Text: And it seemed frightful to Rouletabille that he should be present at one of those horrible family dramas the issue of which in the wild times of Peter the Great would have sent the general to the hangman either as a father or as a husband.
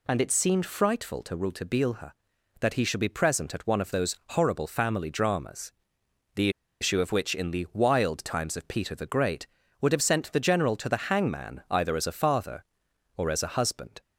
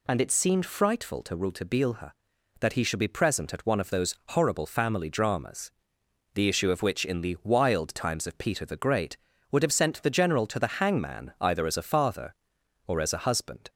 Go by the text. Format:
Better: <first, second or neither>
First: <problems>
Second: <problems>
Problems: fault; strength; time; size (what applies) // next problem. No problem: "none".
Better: second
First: pauses between "dramas" and "the"; noticeable; at 5.7 s; 0.64 s long // pauses between "the" and "issue"; slight; at 6.4 s; 0.31 s long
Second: pauses between "dramas" and "the"; noticeable; at 5.7 s; 0.64 s long